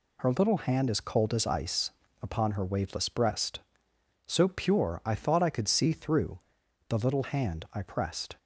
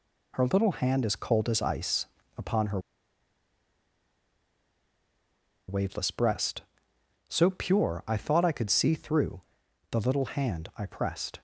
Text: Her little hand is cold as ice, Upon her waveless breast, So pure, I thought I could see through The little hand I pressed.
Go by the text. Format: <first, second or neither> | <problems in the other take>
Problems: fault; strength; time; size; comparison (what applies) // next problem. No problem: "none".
first | pauses between "her" and "waveless"; strong; at 2.8 s; 2.8 s long // pauses between "through" and "The"; noticeable; at 9.4 s; 0.50 s long; noticeable in the first